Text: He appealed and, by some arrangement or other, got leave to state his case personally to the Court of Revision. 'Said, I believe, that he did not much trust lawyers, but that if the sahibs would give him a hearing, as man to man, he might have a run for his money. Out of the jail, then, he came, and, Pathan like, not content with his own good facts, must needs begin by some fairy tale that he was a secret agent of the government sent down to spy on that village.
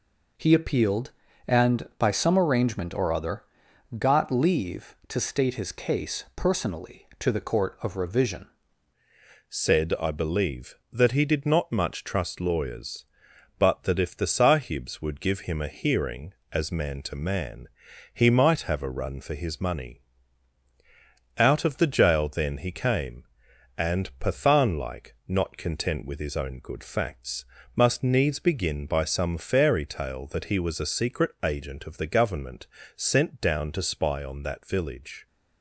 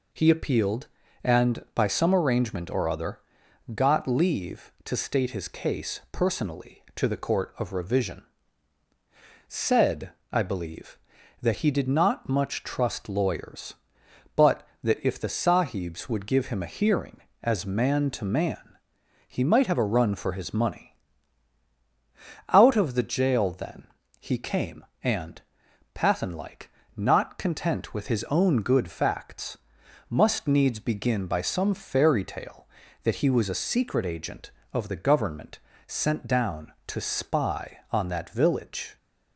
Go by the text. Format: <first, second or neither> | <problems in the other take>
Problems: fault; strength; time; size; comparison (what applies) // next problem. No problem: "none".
second | changes voice at "Said"; from 9.4 s on; 25.8 s long // pauses between "government" and "sent"; slight; at 32.6 s; 0.26 s long; slight in the second